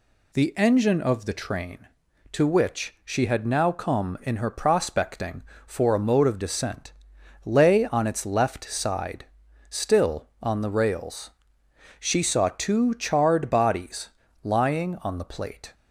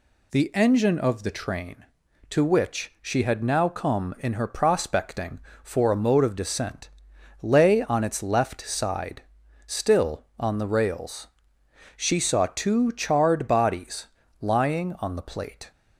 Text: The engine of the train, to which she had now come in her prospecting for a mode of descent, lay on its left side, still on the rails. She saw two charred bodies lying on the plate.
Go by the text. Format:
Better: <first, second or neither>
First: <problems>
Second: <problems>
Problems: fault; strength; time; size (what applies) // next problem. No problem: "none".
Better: neither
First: pauses between "bodies" and "lying"; slight; at 14.0 s; 0.34 s long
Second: pauses between "bodies" and "lying"; slight; at 14.0 s; 0.34 s long